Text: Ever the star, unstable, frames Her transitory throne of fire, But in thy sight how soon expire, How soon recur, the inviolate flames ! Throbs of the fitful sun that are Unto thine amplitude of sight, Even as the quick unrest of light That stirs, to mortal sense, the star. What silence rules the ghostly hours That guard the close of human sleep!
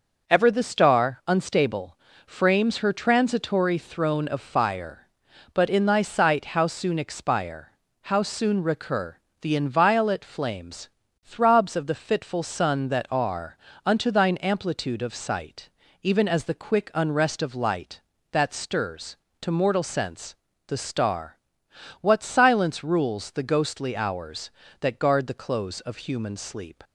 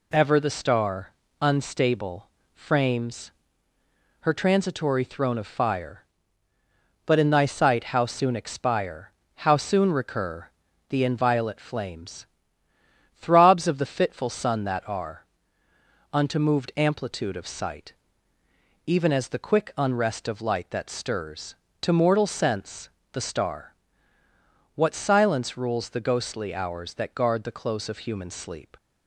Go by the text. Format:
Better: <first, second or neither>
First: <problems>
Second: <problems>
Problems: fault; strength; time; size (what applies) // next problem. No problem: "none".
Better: first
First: pauses between "are" and "Unto"; slight; at 13.5 s; 0.30 s long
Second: pauses between "frames" and "Her"; noticeable; at 3.3 s; 0.90 s long // pauses between "are" and "Unto"; noticeable; at 15.2 s; 0.88 s long // says "moved" for "thine"; at 16.3 s